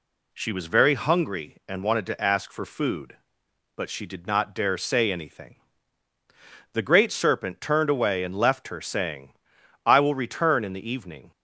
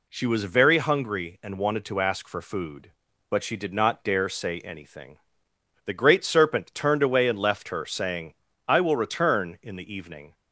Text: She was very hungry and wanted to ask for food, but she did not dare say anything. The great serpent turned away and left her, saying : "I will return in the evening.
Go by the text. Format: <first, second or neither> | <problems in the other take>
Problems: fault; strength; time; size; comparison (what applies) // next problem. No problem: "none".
neither | none